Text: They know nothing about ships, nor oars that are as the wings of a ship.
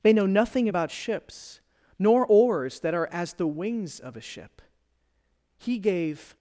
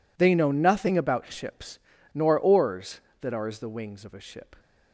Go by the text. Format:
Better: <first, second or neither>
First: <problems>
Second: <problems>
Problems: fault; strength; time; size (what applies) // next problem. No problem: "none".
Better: second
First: goes on to say "He gave"; noticeable; from 5.5 s on; 0.80 s long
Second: none